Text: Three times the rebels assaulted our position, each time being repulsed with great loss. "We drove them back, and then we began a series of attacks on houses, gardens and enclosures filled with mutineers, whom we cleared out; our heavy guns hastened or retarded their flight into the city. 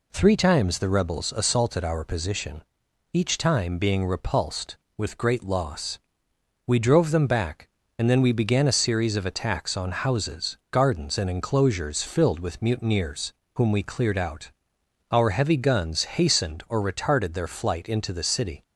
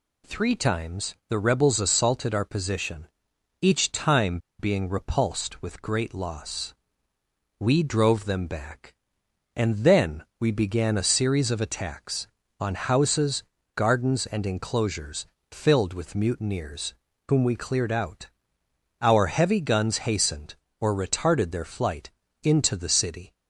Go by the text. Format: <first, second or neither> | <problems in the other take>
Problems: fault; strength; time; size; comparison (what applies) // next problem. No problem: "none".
first | pauses between "time" and "being"; slight; at 4.3 s; 0.21 s long // pauses between "then" and "we"; slight; at 10.2 s; 0.16 s long // pauses between "enclosures" and "filled"; slight; at 15.2 s; 0.26 s long // pauses between "flight" and "into"; slight; at 22.1 s; 0.32 s long